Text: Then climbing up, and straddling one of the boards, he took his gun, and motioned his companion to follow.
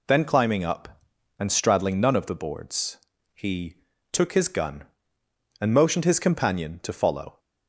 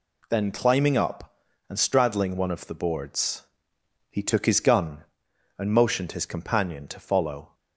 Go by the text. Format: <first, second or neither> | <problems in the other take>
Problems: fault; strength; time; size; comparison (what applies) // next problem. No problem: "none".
second | says "none" for "one"; at 1.9 s // pauses between "he" and "took"; slight; at 3.7 s; 0.36 s long